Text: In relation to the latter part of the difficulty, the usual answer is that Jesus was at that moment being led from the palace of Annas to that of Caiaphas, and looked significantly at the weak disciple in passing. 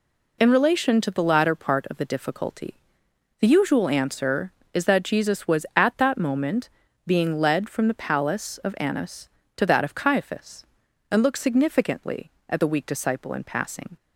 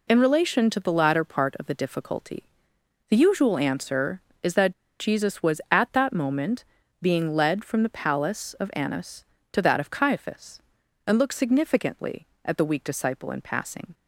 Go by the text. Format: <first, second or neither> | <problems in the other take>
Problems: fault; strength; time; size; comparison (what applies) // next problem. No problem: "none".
first | pauses between "that" and "Jesus"; slight; at 4.7 s; 0.28 s long // pauses between "moment" and "being"; at 6.6 s; 0.38 s long; also in the first